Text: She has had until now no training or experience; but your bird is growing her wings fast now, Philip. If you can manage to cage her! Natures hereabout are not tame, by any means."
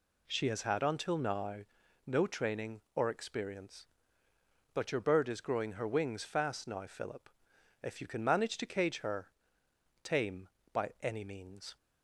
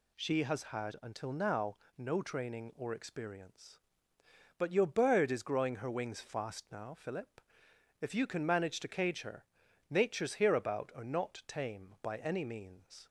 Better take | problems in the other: second | pauses between "now" and "no"; noticeable; at 1.5 s; 0.48 s long; slight in the second // skips "Natures hereabout are not"; at 9.6 s

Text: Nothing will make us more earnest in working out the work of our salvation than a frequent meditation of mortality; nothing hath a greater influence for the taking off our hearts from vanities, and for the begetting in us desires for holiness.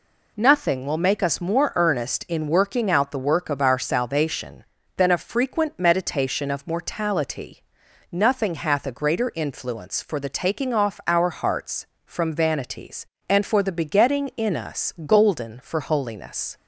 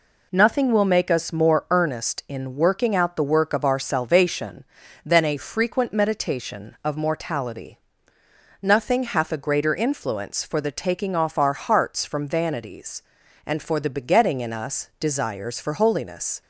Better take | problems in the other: second | says "golden" for "desires"; at 15.0 s

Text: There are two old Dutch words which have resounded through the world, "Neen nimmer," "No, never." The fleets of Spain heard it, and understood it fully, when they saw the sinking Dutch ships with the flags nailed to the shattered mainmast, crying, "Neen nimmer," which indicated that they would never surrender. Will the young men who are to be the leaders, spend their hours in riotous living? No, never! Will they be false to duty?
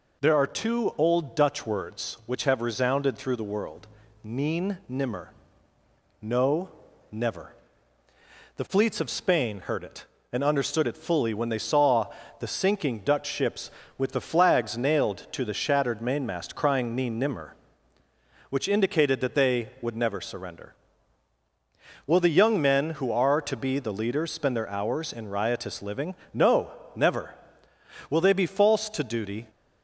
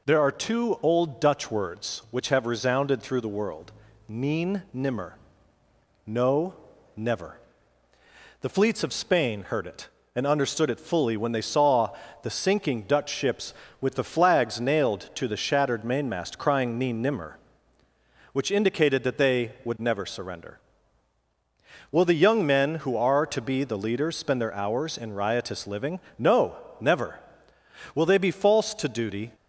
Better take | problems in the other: neither | pauses between "saw" and "the"; slight; the same in both

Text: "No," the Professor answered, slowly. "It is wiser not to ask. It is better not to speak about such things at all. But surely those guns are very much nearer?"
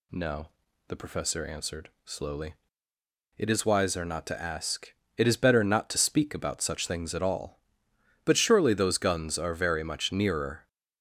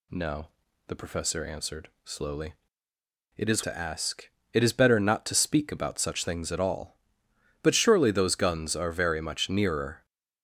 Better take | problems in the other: first | skips "wiser not"; at 3.6 s

